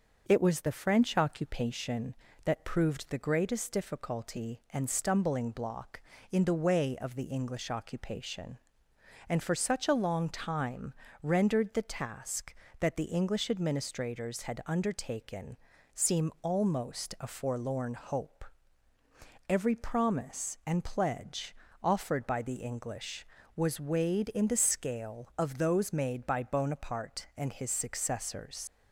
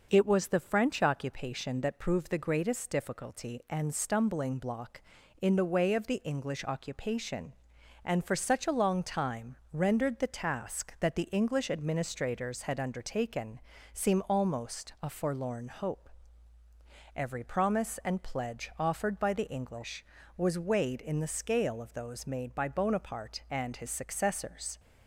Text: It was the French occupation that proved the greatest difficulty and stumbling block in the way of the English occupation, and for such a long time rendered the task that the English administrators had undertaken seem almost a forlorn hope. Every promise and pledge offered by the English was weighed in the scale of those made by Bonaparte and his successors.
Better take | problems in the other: second | starts louder than the rest; noticeable; until 1.2 s; 6 dB // pauses between "time" and "rendered"; slight; at 10.9 s; 0.30 s long; slight in the second // pauses between "undertaken" and "seem"; at 15.5 s; 0.40 s long; slight in the second // pauses between "pledge" and "offered"; slight; at 21.5 s; 0.26 s long // leaves "successors" unfinished; at 28.6 s; 75 ms

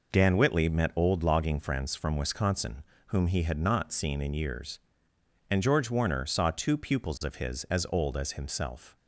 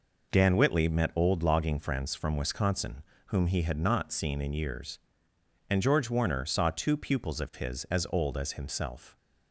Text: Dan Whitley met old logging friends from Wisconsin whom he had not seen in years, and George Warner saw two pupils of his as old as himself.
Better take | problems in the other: neither | pauses between "Wisconsin" and "whom"; slight; the same in both

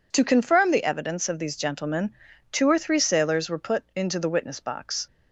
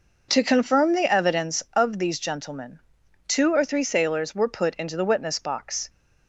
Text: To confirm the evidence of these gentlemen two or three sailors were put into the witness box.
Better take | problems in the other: neither | pauses between "gentlemen" and "two"; the same in both

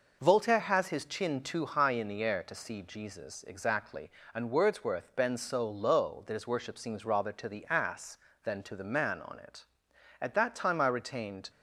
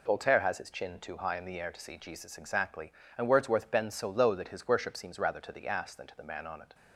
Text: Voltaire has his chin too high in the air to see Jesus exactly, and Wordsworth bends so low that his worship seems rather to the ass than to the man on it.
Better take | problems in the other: second | goes on to say "At that time I retained"; noticeable; from 10.2 s on; 1.2 s long

